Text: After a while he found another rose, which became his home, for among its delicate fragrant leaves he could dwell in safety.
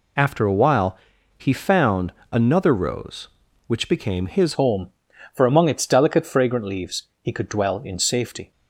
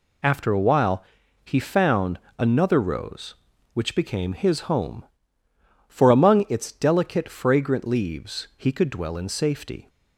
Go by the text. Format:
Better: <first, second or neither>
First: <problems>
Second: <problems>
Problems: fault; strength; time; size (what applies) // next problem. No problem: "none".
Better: second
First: pauses between "while" and "he"; at 0.9 s; 0.40 s long // pauses between "found" and "another"; slight; at 2.1 s; 0.20 s long // changes voice at "home"; from 4.5 s on; 4.0 s long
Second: pauses between "while" and "he"; at 1.0 s; 0.40 s long // pauses between "found" and "another"; slight; at 2.1 s; 0.20 s long